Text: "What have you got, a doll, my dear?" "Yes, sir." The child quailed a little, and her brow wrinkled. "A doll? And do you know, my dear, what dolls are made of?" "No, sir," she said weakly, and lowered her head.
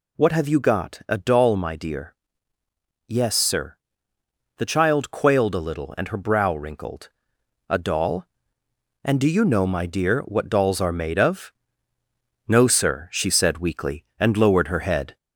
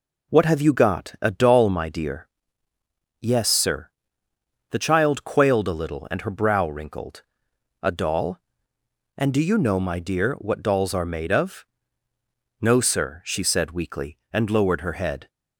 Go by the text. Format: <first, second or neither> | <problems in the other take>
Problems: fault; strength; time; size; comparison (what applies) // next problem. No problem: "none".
second | gets louder; slight; throughout; 2.5 dB